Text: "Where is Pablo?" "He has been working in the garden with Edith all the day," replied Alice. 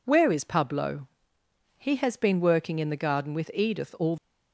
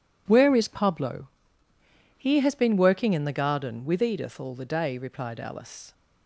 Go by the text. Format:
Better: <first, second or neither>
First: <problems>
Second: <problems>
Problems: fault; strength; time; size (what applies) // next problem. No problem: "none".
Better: second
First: stops before "the day replied Alice"; at 4.1 s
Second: none